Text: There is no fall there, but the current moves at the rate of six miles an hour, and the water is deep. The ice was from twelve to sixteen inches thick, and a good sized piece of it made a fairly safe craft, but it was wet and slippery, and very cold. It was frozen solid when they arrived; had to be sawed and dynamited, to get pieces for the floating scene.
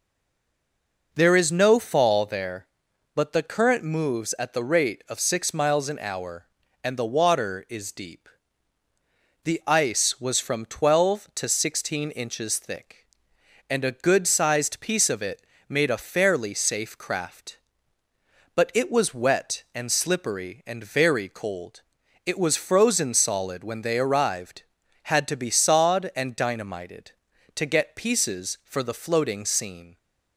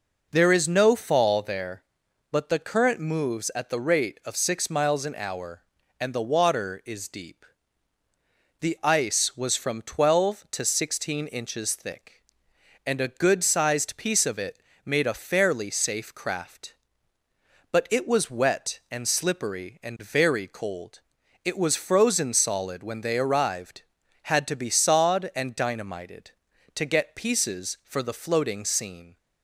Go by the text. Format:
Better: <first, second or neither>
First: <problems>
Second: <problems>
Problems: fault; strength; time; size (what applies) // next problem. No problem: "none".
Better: second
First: stays silent before the first word; until 1.1 s; 1.1 s long // pauses between "it" and "made"; slight; at 15.4 s; 0.24 s long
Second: pauses between "it" and "made"; slight; at 14.6 s; 0.24 s long